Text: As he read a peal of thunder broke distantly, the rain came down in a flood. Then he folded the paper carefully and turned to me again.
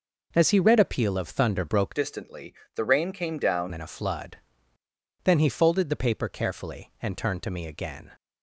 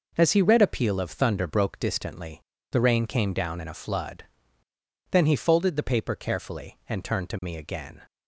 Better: second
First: changes voice from "distantly" to "down"; from 1.9 to 3.7 s; 1.8 s long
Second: none

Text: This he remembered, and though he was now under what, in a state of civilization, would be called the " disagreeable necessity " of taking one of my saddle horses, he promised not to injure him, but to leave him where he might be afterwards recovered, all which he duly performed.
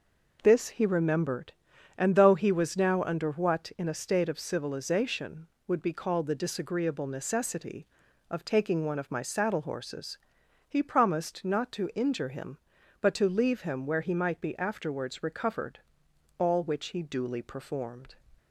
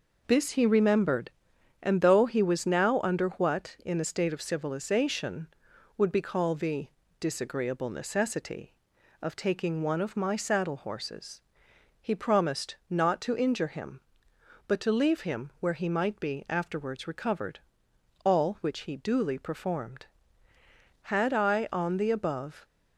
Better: first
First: none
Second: goes on to say "Had I on the above"; from 21.0 s on; 1.5 s long

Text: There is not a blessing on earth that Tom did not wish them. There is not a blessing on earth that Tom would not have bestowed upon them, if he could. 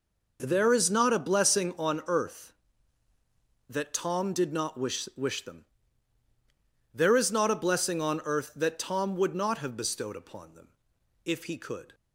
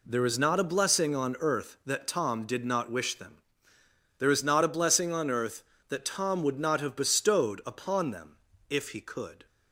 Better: second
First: says "wish" twice; at 5.1 s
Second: none

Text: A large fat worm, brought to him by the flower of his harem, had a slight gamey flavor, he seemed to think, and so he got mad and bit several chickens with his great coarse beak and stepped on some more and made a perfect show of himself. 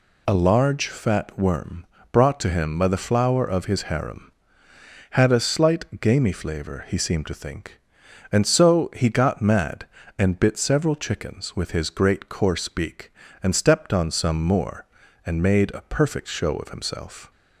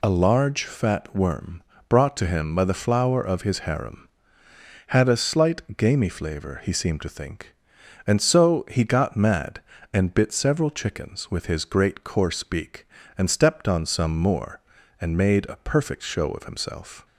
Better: neither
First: none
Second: none

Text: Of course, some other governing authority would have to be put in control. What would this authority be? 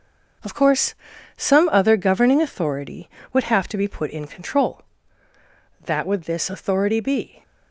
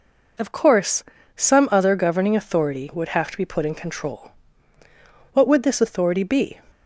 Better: second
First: starts louder than the rest; noticeable; until 1.8 s; 6 dB // says "That" for "What"; at 5.8 s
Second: none

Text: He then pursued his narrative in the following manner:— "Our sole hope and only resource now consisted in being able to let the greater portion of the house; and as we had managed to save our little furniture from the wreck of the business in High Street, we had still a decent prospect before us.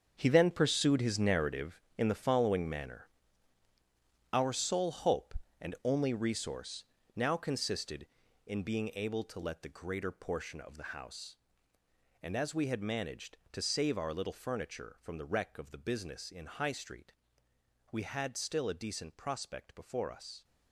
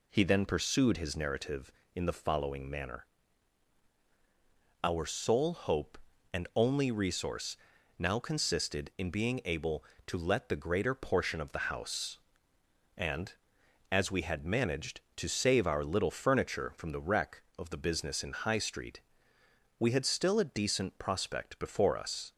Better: second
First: gets quieter; strong; throughout; 12.5 dB // pauses between "resource" and "now"; slight; at 6.8 s; 0.32 s long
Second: pauses between "resource" and "now"; at 7.5 s; 0.42 s long

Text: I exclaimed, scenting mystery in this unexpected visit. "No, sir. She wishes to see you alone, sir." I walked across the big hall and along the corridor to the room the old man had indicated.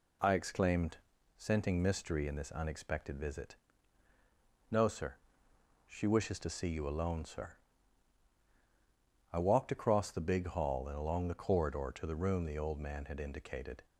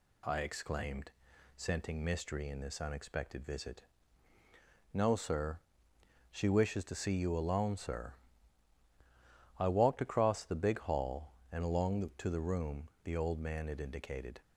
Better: first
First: none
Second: skips "corridor"; at 12.1 s // pauses between "room" and "the"; slight; at 12.8 s; 0.16 s long

